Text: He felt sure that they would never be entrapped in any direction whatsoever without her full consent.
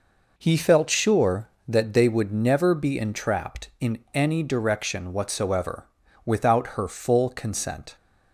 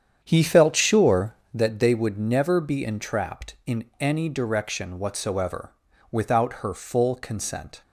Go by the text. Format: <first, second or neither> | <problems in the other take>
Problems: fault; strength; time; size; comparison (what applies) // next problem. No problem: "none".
first | starts louder than the rest; strong; until 1.6 s; 8.5 dB // pauses between "in" and "any"; slight; at 3.8 s; 0.16 s long; slight in the first // pauses between "whatsoever" and "without"; at 5.7 s; 0.38 s long; also in the first